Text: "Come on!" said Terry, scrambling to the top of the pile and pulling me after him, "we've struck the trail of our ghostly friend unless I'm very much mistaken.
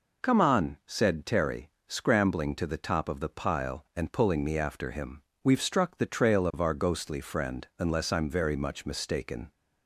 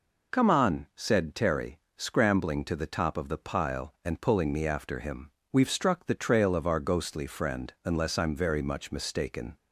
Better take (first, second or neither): neither